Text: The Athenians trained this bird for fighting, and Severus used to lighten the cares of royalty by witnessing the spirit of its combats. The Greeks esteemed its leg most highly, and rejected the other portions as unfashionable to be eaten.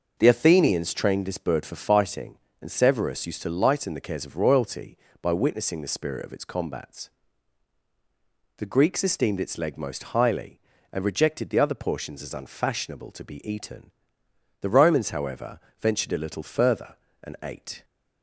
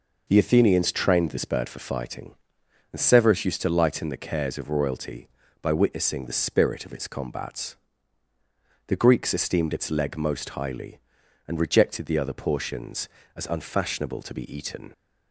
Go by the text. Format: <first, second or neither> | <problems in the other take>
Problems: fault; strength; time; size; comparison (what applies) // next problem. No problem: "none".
second | goes on to say "The Romans however ventured a little further and ate"; strong; from 14.6 s on; 3.2 s long